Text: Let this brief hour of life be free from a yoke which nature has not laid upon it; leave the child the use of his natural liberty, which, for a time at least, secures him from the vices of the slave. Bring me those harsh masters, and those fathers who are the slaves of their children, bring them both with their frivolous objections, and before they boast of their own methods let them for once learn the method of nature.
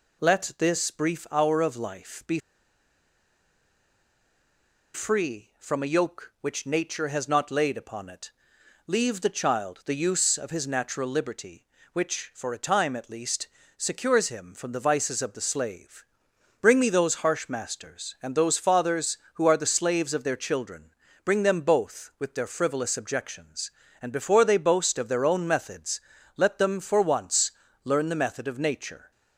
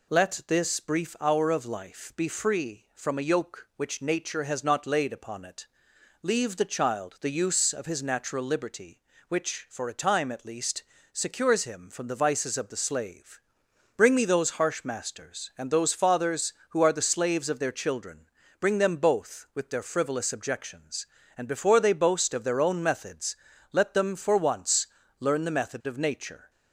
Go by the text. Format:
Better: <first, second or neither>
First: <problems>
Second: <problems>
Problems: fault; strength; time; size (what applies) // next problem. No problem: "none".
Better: second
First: pauses between "be" and "free"; strong; at 2.3 s; 2.5 s long // pauses between "methods" and "let"; slight; at 26.0 s; 0.36 s long // pauses between "once" and "learn"; slight; at 27.5 s; 0.34 s long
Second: pauses between "methods" and "let"; slight; at 23.3 s; 0.36 s long // pauses between "once" and "learn"; slight; at 24.8 s; 0.34 s long